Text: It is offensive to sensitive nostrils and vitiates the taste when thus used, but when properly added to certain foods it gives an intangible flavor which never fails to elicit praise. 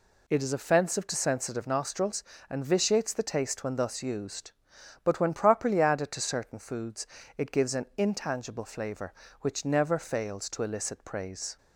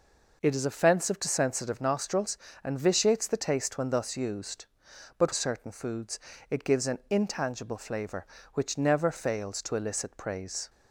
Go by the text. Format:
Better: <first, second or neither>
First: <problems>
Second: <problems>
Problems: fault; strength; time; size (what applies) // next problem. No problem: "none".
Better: first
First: pauses between "foods" and "it"; slight; at 7.0 s; 0.30 s long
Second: skips "when properly added to"; at 5.3 s // pauses between "foods" and "it"; slight; at 6.1 s; 0.30 s long